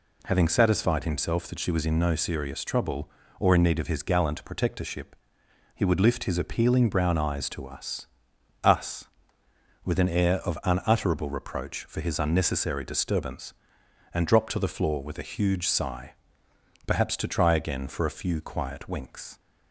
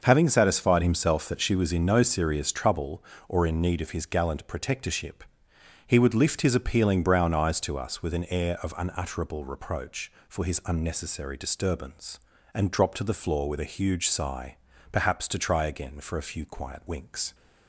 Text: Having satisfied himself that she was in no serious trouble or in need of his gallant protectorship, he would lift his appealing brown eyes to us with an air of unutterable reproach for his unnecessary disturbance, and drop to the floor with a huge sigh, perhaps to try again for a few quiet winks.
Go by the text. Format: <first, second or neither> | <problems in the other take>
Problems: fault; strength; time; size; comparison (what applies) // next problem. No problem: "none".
second | says "us" twice; at 8.6 s